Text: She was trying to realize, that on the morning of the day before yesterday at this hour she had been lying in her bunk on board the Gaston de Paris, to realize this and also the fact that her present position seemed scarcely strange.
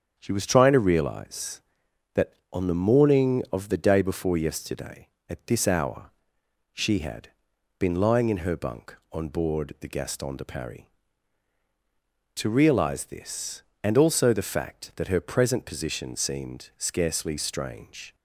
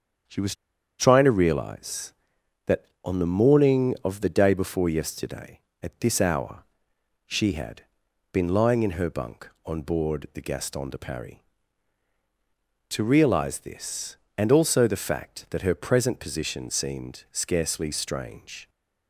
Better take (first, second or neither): first